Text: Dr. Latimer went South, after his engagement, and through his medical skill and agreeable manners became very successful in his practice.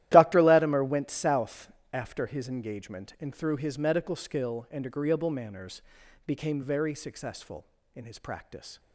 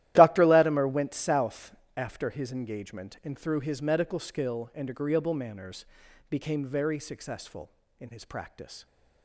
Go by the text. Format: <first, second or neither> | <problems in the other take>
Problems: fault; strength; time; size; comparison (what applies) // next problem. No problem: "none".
neither | starts louder than the rest; strong; the same in both // pauses between "manners" and "became"; noticeable; the same in both